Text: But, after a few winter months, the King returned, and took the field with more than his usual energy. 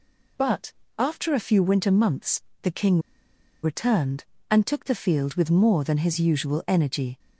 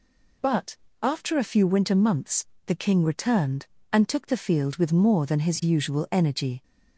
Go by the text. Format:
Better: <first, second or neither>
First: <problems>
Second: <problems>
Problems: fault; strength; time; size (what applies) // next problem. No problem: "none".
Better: second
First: pauses between "King" and "returned"; noticeable; at 2.9 s; 0.64 s long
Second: none